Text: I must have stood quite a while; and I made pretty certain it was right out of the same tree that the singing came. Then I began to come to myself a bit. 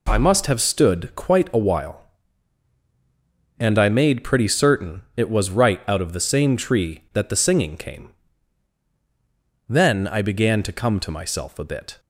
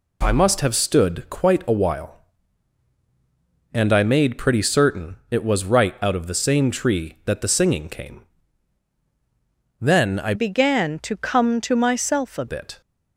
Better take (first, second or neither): first